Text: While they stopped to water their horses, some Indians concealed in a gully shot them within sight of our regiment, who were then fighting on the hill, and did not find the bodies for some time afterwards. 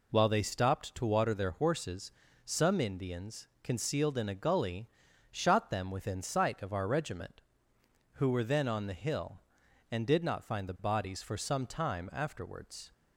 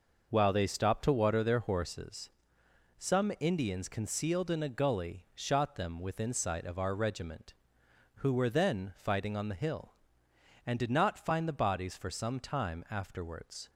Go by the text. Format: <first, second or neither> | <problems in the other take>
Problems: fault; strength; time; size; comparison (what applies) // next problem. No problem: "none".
second | pauses between "gully" and "shot"; at 4.8 s; 0.42 s long // skips "fighting"; at 8.6 s